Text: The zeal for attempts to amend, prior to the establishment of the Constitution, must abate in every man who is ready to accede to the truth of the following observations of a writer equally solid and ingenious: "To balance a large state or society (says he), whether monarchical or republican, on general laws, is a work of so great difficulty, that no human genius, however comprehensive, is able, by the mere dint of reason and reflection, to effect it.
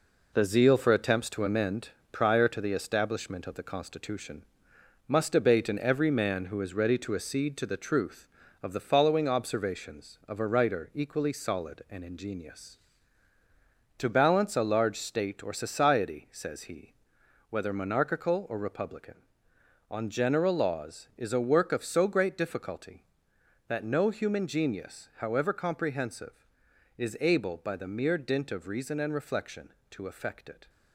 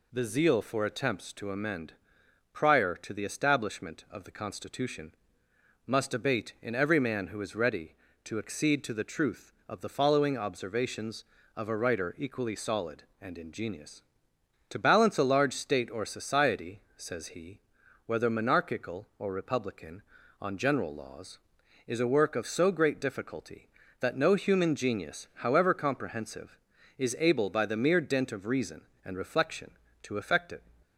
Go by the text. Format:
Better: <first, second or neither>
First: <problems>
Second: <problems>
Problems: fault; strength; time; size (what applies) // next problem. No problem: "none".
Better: second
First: gets quieter; throughout; 7 dB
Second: none